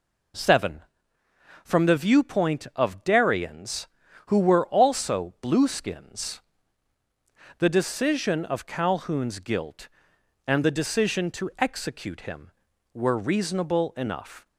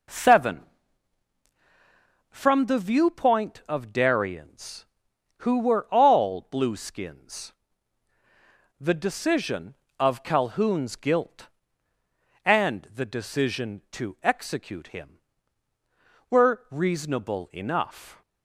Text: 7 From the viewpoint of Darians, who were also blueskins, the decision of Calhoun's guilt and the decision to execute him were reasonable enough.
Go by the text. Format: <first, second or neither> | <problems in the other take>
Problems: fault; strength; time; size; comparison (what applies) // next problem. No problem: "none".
first | says "all" for "also"; at 5.9 s